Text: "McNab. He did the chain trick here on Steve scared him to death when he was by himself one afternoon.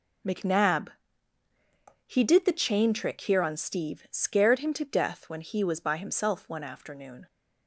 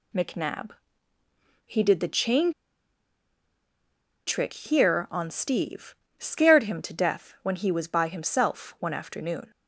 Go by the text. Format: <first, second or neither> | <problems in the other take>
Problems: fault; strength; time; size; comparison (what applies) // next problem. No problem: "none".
first | pauses between "chain" and "trick"; strong; at 2.5 s; 1.7 s long // pauses between "Steve" and "scared"; slight; at 5.9 s; 0.20 s long